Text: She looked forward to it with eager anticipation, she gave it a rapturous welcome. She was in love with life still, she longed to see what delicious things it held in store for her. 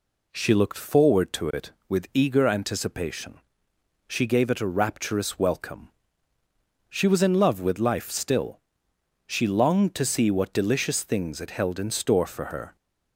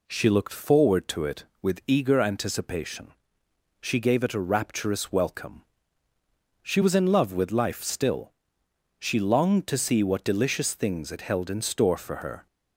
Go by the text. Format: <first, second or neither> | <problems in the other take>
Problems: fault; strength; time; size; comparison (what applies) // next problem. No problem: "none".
neither | none